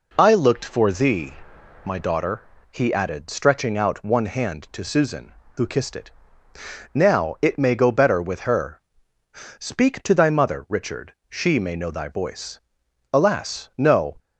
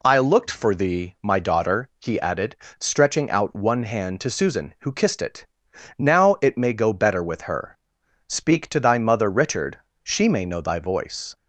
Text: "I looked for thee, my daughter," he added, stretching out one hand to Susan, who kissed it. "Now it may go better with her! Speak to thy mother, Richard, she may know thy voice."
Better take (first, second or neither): second